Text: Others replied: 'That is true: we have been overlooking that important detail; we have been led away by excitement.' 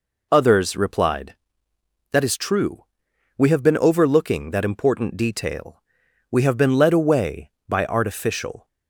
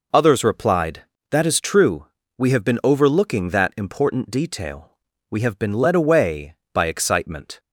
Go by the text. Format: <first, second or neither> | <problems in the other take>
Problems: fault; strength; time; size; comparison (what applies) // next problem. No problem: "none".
second | says "artificial" for "excitement"; at 7.8 s